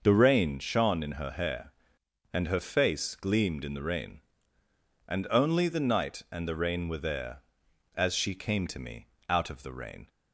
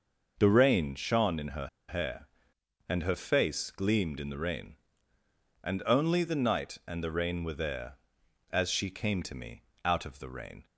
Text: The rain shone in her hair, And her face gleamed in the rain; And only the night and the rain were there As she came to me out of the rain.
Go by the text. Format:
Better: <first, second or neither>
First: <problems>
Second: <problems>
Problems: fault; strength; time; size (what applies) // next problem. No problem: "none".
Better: first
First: pauses between "me" and "out"; slight; at 9.0 s; 0.20 s long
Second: pauses between "her" and "hair"; slight; at 1.6 s; 0.20 s long // pauses between "me" and "out"; slight; at 9.6 s; 0.20 s long